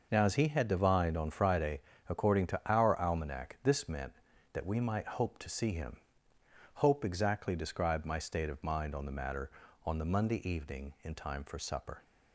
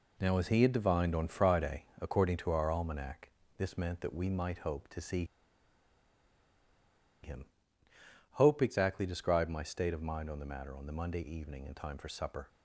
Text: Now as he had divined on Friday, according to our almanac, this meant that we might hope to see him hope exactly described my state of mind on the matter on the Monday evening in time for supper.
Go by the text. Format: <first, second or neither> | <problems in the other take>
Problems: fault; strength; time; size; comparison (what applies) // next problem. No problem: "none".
first | pauses between "see" and "him"; strong; at 5.2 s; 1.9 s long // pauses between "him" and "hope"; noticeable; at 7.4 s; 0.90 s long; noticeable in the first